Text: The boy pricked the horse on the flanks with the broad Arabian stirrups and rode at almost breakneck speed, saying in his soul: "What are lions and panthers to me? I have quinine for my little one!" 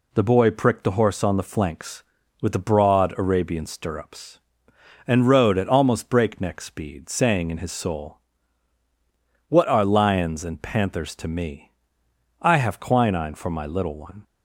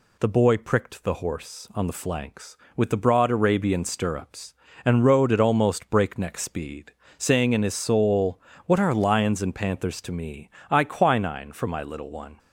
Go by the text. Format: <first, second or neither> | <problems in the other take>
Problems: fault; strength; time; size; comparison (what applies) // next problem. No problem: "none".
first | skips "have"; at 10.8 s